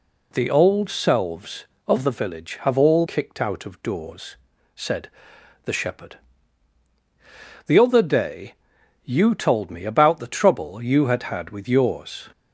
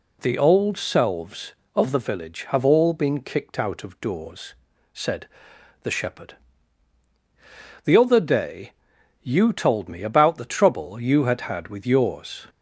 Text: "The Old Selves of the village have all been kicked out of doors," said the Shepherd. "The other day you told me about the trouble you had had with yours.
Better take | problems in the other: second | skips "been"; at 3.0 s // pauses between "said" and "the"; noticeable; at 5.1 s; 0.54 s long; noticeable in the second // pauses between "day" and "you"; noticeable; at 8.5 s; 0.50 s long; noticeable in the second

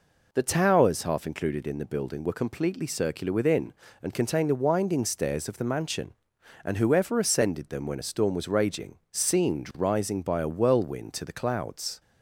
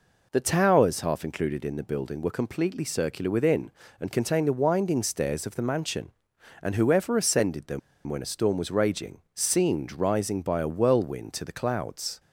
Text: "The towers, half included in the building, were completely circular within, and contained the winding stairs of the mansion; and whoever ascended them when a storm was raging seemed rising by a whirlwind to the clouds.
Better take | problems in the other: first | pauses between "them" and "when"; slight; at 7.7 s; 0.27 s long

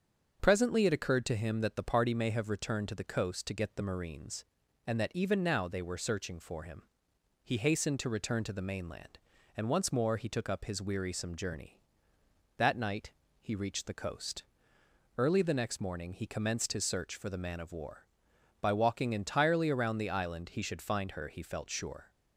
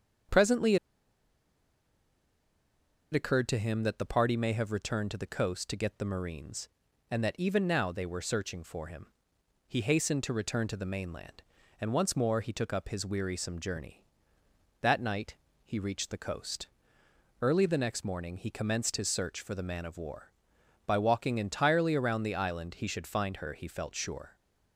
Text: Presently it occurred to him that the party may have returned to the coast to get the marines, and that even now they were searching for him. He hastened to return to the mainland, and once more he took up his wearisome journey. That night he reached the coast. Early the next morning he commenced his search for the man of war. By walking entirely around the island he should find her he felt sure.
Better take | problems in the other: first | starts louder than the rest; until 3.6 s; 7 dB; also in the first // pauses between "Presently" and "it"; strong; at 0.7 s; 2.3 s long // pauses between "night" and "he"; slight; at 15.3 s; 0.30 s long; slight in the first

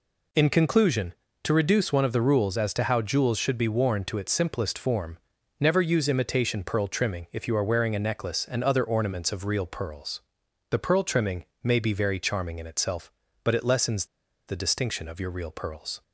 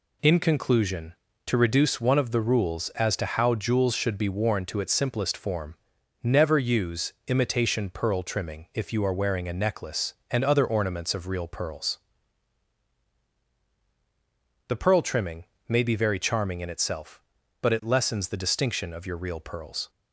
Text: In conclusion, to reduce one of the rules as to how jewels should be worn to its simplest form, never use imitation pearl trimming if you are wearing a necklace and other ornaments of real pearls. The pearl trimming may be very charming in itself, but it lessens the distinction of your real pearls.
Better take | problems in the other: second | pauses between "trimming" and "may"; slight; at 11.4 s; 0.20 s long; slight in the second // pauses between "lessens" and "the"; at 14.0 s; 0.42 s long

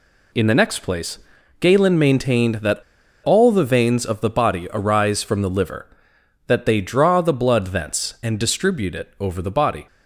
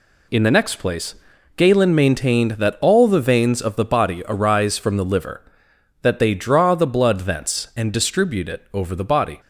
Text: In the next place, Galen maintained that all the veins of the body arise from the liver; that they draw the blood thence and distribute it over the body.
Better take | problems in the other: second | pauses between "that" and "all"; at 2.7 s; 0.44 s long

